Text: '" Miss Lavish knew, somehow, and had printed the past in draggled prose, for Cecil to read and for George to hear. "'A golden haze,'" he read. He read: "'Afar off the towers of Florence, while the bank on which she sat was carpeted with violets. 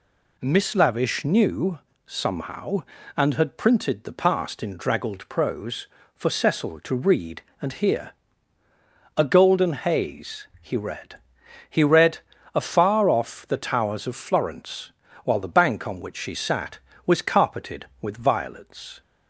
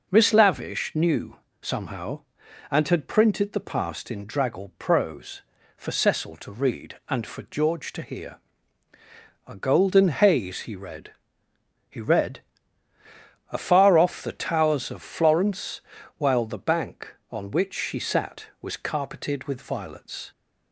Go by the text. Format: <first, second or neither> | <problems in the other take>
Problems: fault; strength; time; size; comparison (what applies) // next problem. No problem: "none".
second | skips "for George to"; at 7.7 s